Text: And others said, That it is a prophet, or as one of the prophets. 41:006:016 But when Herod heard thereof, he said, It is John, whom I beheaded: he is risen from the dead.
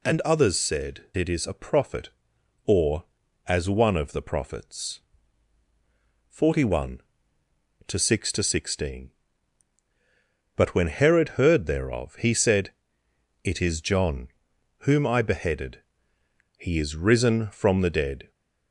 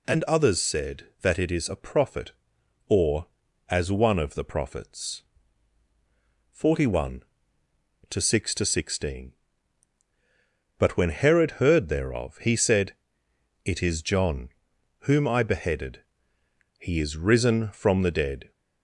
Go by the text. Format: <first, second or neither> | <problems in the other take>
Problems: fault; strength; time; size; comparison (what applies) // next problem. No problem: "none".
second | skips "That"; at 1.1 s